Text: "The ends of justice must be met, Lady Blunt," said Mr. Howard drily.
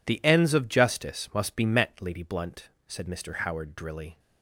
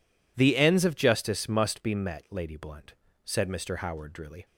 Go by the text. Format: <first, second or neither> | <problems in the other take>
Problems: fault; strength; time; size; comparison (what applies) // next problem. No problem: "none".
neither | none